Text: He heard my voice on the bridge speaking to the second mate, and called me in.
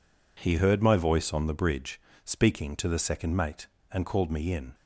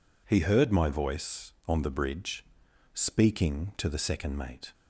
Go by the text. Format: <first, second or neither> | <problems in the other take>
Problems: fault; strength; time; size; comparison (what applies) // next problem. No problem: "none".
first | pauses between "bridge" and "speaking"; noticeable; at 2.4 s; 0.50 s long; slight in the first // stops before "and called me in"; at 4.7 s